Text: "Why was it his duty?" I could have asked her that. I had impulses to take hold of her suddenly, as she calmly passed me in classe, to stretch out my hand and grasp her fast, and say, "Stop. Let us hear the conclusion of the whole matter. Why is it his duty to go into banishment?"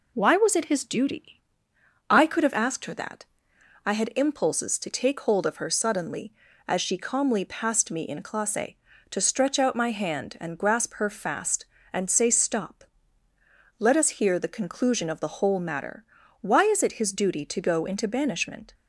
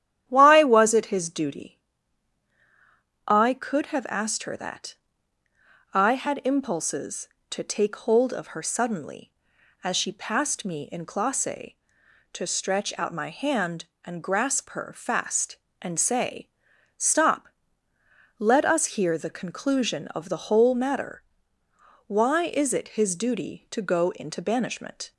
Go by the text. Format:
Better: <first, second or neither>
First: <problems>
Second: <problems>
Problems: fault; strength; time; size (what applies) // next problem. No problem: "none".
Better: first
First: none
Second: starts louder than the rest; strong; until 1.2 s; 11 dB // skips "calmly"; at 10.1 s